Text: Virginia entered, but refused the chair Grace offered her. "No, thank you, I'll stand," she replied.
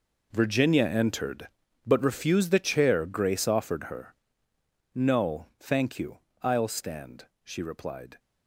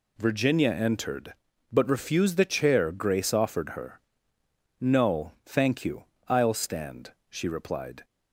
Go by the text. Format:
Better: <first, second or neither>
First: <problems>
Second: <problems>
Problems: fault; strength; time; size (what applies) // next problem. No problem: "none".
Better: second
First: gets quieter; strong; throughout; 13.5 dB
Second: none